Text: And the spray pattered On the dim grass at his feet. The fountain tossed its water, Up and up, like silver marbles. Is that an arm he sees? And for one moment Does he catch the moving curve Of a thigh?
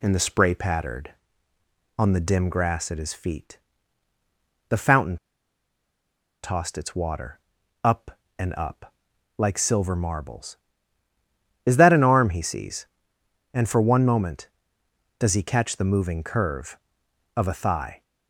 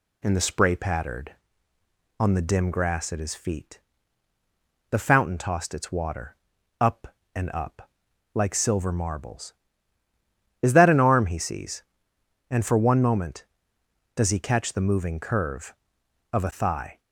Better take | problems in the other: second | pauses between "fountain" and "tossed"; strong; at 5.1 s; 1.2 s long

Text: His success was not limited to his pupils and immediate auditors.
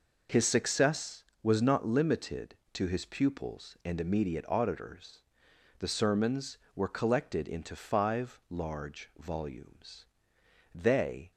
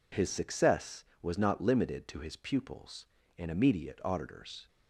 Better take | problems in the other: second | goes on to say "The sermons were collected into five large volumes they"; strong; from 5.7 s on; 5.5 s long

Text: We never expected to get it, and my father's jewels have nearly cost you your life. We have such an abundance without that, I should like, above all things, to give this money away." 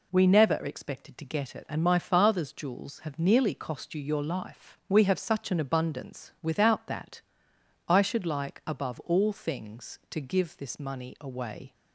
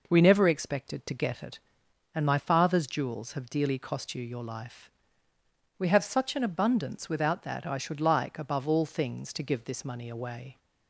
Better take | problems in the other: first | says "dearly" for "nearly"; at 3.5 s

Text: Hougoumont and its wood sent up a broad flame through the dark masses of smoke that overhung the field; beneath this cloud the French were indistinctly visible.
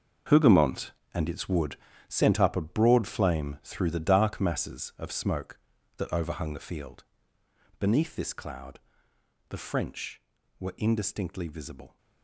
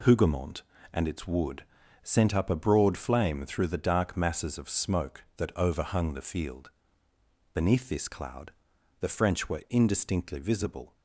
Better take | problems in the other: second | gets quieter; strong; throughout; 12.5 dB // pauses between "wood" and "sent"; slight; at 1.7 s; 0.32 s long; also in the second // pauses between "cloud" and "the"; noticeable; at 8.8 s; 0.68 s long; noticeable in the second

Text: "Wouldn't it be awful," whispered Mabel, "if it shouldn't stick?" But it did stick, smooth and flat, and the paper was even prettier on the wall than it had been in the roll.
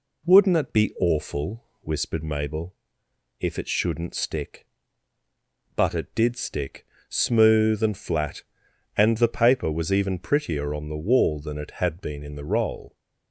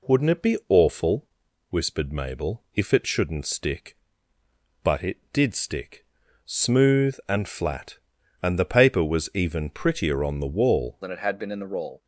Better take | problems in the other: first | changes voice at "than"; from 11.0 s on; 1.0 s long

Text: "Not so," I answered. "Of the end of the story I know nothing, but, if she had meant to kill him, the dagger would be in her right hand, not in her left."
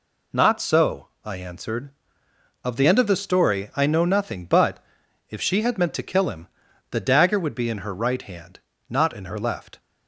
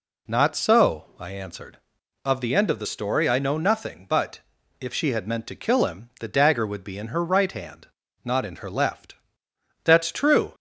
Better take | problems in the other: first | goes on to say "That's true"; noticeable; from 9.8 s on; 0.70 s long

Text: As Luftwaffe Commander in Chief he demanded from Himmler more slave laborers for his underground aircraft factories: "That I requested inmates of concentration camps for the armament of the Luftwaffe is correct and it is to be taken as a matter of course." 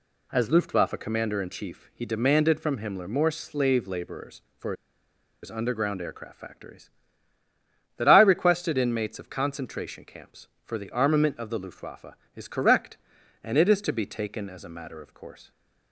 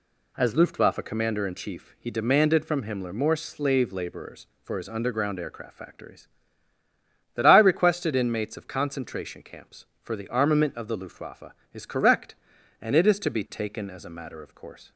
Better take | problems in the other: second | pauses between "for" and "his"; noticeable; at 4.7 s; 0.69 s long

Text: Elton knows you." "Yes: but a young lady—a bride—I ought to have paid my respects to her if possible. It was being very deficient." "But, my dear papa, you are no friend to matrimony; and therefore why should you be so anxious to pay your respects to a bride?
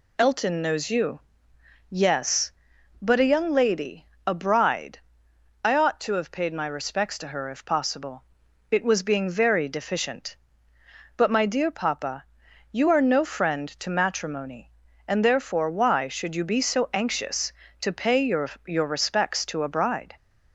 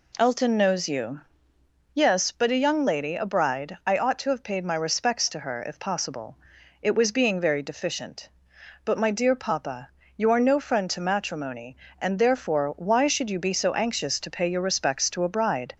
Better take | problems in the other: second | says "your" twice; at 18.6 s

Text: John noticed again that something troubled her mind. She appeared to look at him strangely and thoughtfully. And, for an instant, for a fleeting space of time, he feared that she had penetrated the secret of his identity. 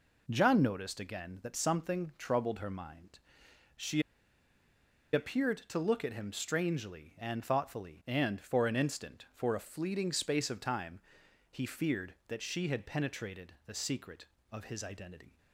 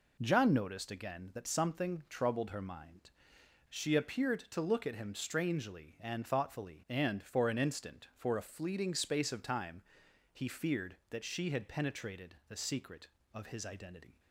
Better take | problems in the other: second | pauses between "She" and "appeared"; at 4.0 s; 1.1 s long

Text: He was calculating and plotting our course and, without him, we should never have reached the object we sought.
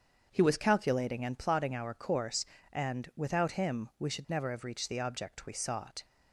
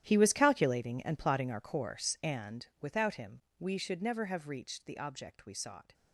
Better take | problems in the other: first | gets quieter; strong; throughout; 16.5 dB // starts louder than the rest; strong; until 1.0 s; 11.5 dB; strong in the first

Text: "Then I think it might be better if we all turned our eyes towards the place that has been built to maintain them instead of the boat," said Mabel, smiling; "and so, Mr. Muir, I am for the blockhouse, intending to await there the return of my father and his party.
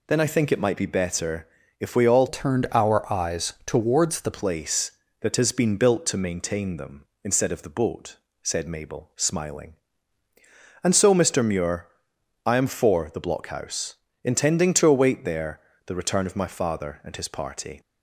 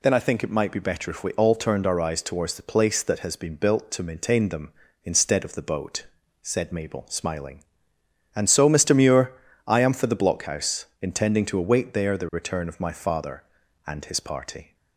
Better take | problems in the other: second | pauses between "better" and "if"; slight; at 1.4 s; 0.32 s long // changes voice from "turned" to "the"; from 2.2 to 4.3 s; 2.1 s long // pauses between "there" and "the"; slight; at 15.5 s; 0.28 s long

